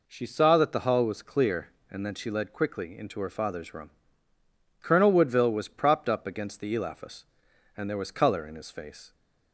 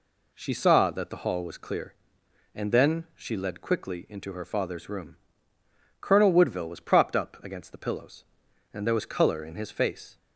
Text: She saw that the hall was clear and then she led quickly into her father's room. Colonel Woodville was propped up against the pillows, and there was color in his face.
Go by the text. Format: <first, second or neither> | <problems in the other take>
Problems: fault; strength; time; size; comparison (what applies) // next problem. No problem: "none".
second | says "elaphus" for "pillows"; at 6.7 s